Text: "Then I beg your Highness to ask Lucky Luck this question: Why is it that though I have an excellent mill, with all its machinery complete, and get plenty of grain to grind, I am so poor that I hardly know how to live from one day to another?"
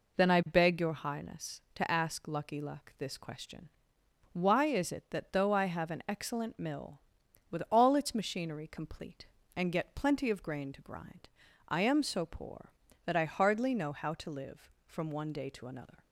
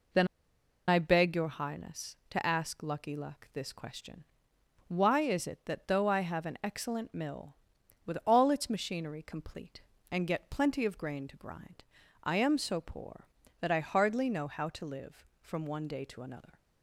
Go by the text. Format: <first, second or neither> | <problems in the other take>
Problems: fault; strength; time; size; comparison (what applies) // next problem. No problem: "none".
first | pauses between "Then" and "I"; noticeable; at 0.2 s; 0.61 s long